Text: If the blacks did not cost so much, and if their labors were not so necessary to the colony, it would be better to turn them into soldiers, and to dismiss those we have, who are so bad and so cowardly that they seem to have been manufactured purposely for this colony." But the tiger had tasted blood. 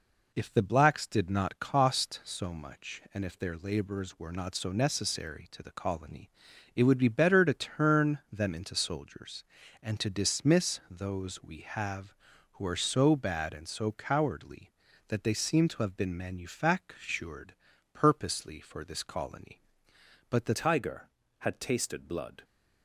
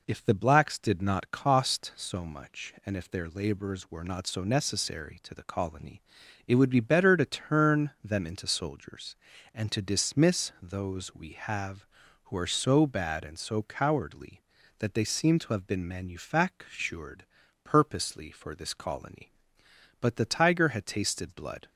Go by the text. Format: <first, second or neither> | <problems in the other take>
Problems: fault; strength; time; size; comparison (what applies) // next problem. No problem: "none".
second | pauses between "manufactured" and "purposely"; at 17.5 s; 0.40 s long; also in the second // changes voice at "tiger"; from 20.5 s on; 1.9 s long